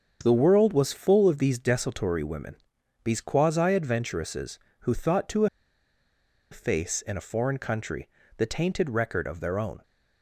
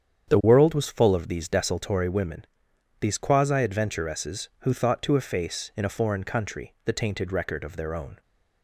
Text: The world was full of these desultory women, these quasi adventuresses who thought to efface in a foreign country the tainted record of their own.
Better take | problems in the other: second | starts louder than the rest; until 1.2 s; 7 dB; strong in the second // pauses between "to" and "efface"; at 5.4 s; 1.0 s long // pauses between "country" and "the"; slight; at 8.0 s; 0.28 s long

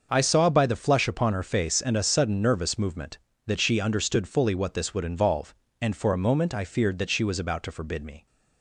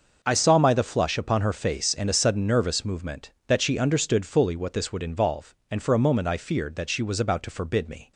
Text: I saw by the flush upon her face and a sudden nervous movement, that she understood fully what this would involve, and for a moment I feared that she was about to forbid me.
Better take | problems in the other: first | starts louder than the rest; until 1.2 s; 6 dB; also in the first // says "my" for "by"; at 0.5 s

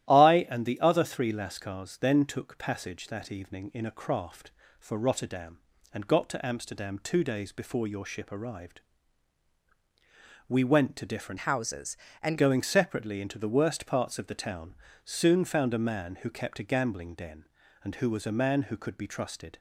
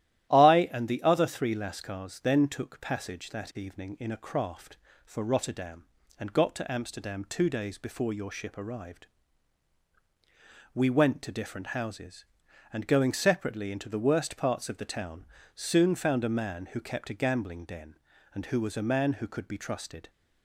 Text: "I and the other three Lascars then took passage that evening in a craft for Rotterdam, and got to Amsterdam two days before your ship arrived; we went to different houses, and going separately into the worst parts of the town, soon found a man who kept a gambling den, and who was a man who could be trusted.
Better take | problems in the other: second | starts louder than the rest; strong; until 1.1 s; 13 dB; strong in the second // changes voice from "houses" to "and"; from 11.3 to 12.3 s; 1.0 s long

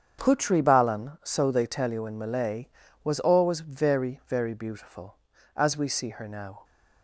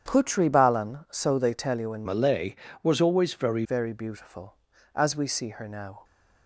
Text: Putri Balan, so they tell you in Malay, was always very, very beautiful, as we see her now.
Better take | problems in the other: first | starts louder than the rest; strong; until 1.1 s; 8.5 dB; strong in the first // changes voice from "Malay" to "very"; from 2.0 to 3.6 s; 1.6 s long

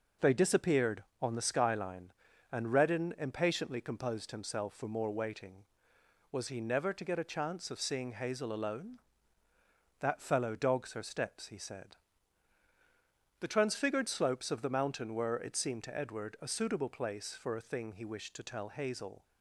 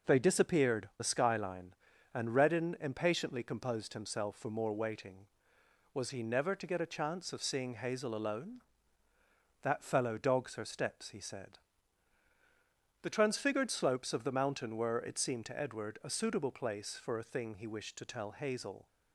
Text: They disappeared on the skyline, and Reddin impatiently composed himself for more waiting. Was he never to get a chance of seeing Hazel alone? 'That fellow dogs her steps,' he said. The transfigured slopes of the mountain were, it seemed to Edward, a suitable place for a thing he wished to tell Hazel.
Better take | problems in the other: first | skips "on"; at 0.9 s

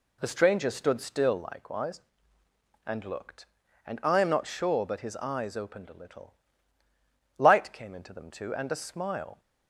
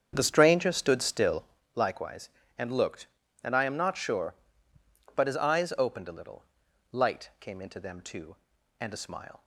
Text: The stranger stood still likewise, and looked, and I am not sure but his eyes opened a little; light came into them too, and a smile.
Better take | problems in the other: first | starts louder than the rest; strong; until 1.7 s; 7.5 dB // pauses between "still" and "likewise"; slight; at 1.4 s; 0.32 s long

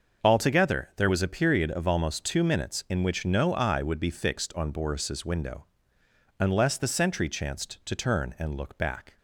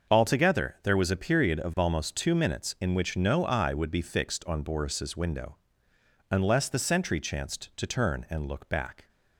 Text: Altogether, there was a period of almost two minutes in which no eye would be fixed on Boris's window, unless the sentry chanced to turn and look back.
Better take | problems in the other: neither | starts louder than the rest; the same in both

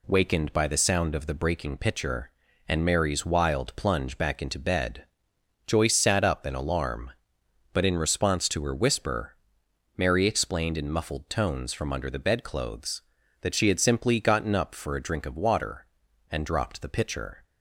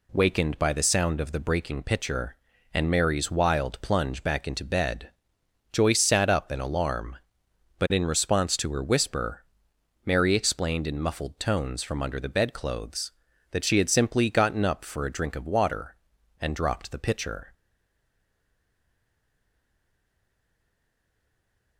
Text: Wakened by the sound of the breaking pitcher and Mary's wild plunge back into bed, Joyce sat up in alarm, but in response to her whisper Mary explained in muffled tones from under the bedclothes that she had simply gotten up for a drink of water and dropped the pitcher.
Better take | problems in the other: first | pauses between "whisper" and "Mary"; noticeable; at 9.4 s; 0.62 s long; noticeable in the first // stays silent after the last word; strong; from 17.5 s on; 4.2 s long

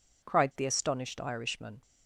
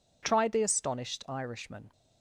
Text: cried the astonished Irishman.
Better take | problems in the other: first | says "tried" for "cried"; at 0.2 s

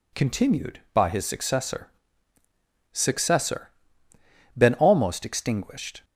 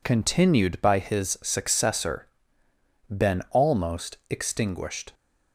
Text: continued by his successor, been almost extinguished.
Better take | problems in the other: second | says "successor" twice; at 2.9 s

